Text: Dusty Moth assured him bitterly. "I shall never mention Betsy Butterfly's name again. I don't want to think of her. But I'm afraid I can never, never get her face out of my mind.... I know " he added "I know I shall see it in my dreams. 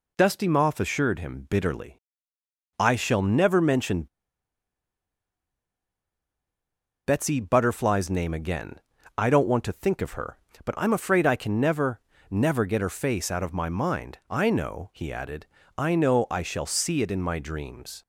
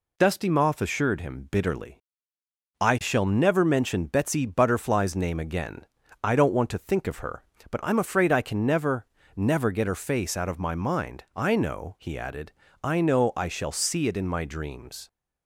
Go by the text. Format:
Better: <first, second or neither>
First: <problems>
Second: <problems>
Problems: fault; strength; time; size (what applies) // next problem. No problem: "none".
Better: second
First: pauses between "mention" and "Betsy"; strong; at 4.0 s; 2.9 s long // pauses between "added" and "I"; slight; at 15.4 s; 0.32 s long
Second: pauses between "added" and "I"; slight; at 12.5 s; 0.32 s long